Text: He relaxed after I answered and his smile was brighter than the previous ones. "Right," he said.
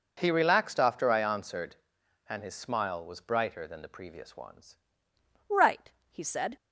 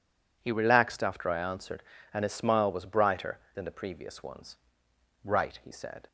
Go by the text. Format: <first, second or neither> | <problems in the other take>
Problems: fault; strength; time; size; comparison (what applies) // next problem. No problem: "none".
second | changes voice at "Right"; from 5.4 s on; 1.1 s long